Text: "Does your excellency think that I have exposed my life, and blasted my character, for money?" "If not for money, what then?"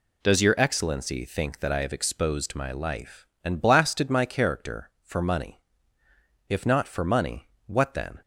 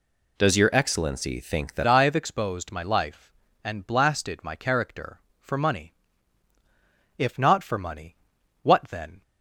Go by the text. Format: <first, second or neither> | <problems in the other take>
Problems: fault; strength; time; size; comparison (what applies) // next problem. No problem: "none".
first | changes voice at "I"; from 1.8 s on; 7.4 s long